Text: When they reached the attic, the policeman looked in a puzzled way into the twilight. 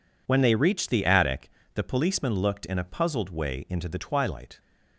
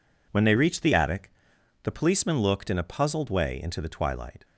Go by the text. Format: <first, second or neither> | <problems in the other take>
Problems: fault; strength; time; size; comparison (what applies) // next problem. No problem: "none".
neither | none